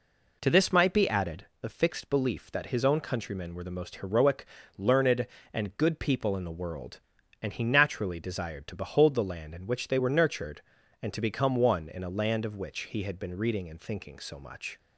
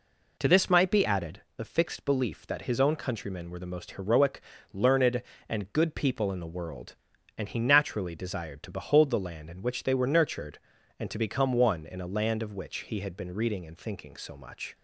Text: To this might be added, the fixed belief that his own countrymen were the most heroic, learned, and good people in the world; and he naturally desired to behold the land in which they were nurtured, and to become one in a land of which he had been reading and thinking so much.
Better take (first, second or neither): neither